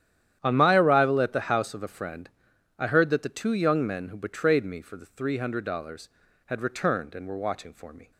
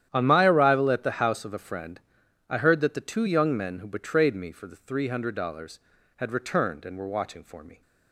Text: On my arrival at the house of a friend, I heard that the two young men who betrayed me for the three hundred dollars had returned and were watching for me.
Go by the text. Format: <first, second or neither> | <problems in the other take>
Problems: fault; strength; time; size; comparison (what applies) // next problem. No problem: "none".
neither | starts louder than the rest; strong; the same in both